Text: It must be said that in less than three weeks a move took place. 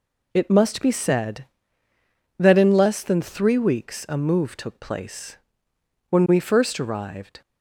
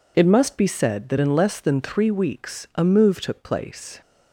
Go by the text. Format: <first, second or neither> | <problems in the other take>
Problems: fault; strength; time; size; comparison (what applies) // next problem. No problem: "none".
second | goes on to say "When we first arrived"; noticeable; from 6.1 s on; 1.3 s long